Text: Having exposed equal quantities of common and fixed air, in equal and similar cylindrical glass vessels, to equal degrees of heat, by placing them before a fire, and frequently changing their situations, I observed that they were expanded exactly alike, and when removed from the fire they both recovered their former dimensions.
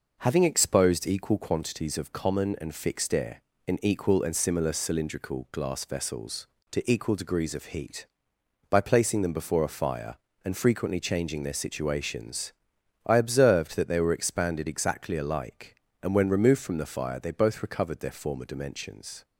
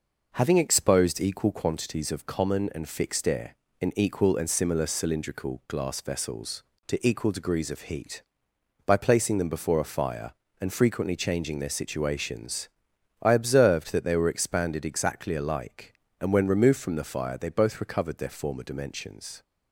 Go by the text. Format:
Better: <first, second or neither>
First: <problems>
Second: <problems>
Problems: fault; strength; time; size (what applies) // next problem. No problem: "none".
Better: neither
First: none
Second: none